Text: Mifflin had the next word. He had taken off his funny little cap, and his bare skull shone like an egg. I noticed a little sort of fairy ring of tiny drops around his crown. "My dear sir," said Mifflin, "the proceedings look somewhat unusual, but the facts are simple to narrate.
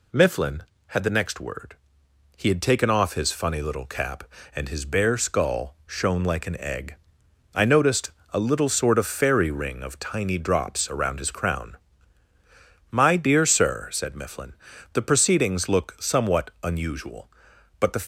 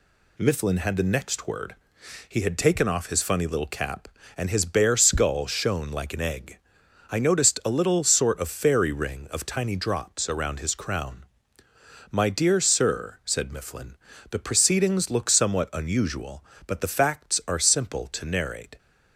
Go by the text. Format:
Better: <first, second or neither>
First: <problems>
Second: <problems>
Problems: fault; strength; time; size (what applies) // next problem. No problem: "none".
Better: second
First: pauses between "noticed" and "a"; slight; at 8.1 s; 0.22 s long // stops before "facts are simple to narrate"; at 18.0 s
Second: none